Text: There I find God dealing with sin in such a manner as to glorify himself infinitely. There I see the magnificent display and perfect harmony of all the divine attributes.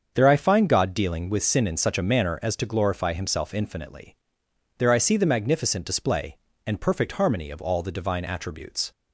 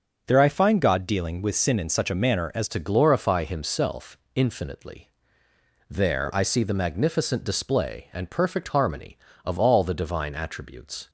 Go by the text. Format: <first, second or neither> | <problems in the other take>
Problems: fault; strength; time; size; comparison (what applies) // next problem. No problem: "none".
first | starts louder than the rest; until 1.2 s; 6.5 dB; also in the first // changes voice at "to"; from 2.6 s on; 8.4 s long // pauses between "himself" and "infinitely"; slight; at 4.1 s; 0.16 s long